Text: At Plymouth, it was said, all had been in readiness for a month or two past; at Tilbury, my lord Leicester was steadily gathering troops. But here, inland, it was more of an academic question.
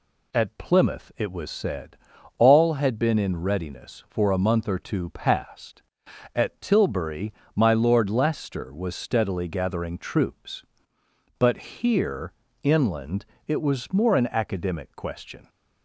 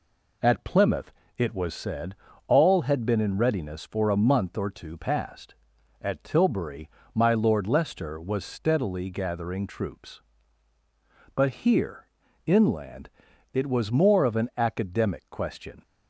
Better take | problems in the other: second | skips "of"; at 14.1 s

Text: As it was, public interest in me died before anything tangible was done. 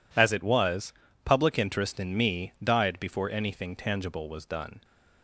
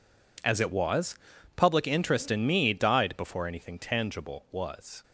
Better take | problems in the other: first | stops before "done"; at 5.0 s

